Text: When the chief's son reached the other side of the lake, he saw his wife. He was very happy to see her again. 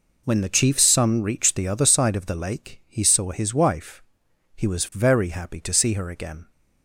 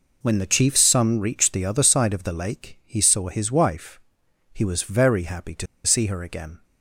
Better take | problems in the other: first | pauses between "to" and "see"; slight; at 5.6 s; 0.18 s long

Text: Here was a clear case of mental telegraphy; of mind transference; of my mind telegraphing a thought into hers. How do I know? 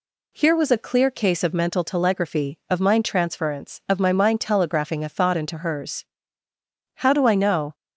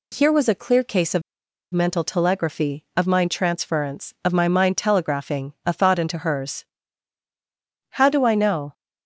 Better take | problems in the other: first | pauses between "of" and "mental"; noticeable; at 1.2 s; 0.51 s long

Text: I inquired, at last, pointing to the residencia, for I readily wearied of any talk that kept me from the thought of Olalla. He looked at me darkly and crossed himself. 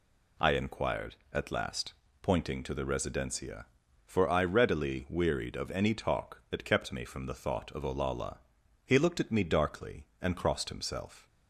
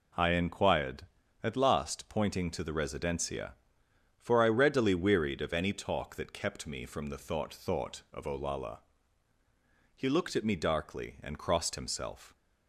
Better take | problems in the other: first | says "thought" twice; at 7.5 s

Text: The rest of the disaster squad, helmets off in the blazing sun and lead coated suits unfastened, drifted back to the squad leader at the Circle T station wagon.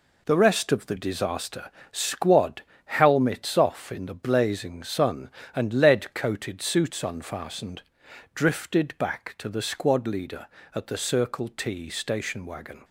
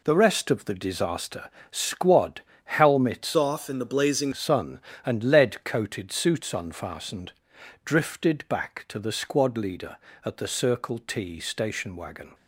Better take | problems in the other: first | pauses between "disaster" and "squad"; slight; at 1.5 s; 0.20 s long; slight in the first // changes voice from "off" to "blazing"; from 3.3 to 4.3 s; 1.0 s long

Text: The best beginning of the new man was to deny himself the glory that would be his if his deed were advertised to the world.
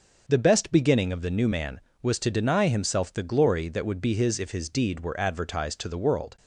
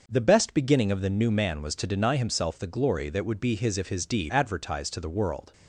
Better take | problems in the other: first | starts louder than the rest; noticeable; until 1.0 s; 6 dB; also in the first // skips "were"; at 4.3 s

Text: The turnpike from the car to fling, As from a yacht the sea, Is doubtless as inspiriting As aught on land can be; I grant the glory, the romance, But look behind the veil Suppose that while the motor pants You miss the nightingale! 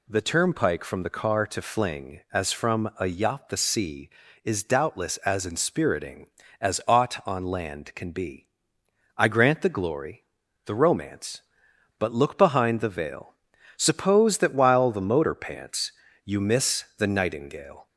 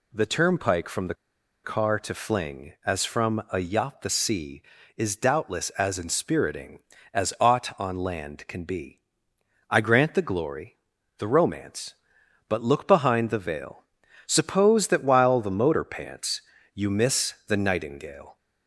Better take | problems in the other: first | pauses between "the" and "car"; noticeable; at 1.1 s; 0.49 s long // pauses between "veil" and "Suppose"; at 13.8 s; 0.44 s long; also in the first // pauses between "pants" and "You"; slight; at 16.4 s; 0.32 s long; slight in the first // pauses between "miss" and "the"; slight; at 17.3 s; 0.16 s long; slight in the first

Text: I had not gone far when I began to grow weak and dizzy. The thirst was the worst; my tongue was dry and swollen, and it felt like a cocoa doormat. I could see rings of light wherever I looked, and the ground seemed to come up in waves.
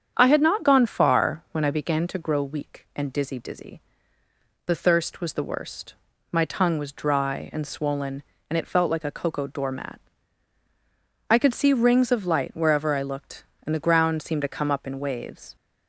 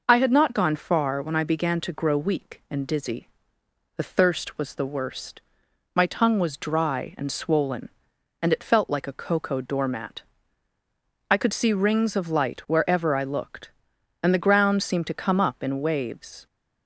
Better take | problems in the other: second | starts louder than the rest; strong; until 1.1 s; 8 dB // says "dizzy" twice; at 3.3 s

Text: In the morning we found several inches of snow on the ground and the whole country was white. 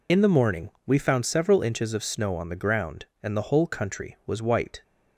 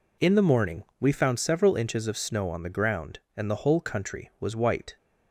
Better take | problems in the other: second | loses the start of "In"; at 0.0 s; 35 ms // pauses between "morning" and "we"; slight; at 0.6 s; 0.16 s long; slight in the second

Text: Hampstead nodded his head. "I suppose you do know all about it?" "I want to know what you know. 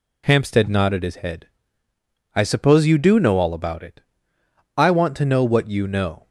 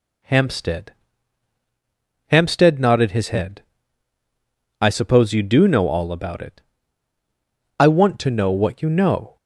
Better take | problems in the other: first | says "Hampstead" twice; at 2.2 s

